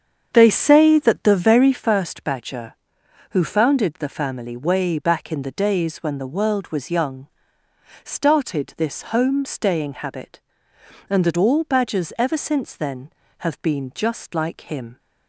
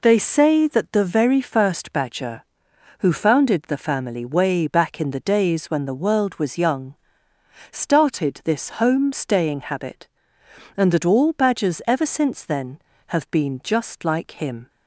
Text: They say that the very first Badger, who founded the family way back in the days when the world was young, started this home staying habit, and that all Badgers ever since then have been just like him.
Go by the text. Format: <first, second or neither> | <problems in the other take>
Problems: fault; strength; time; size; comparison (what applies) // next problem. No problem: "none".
second | starts louder than the rest; strong; until 1.9 s; 7.5 dB